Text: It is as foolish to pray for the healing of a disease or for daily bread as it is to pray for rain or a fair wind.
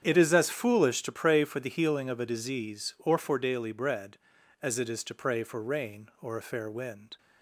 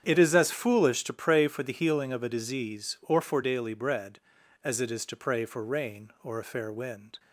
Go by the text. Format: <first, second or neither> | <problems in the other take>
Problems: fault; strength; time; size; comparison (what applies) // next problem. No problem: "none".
neither | starts louder than the rest; strong; the same in both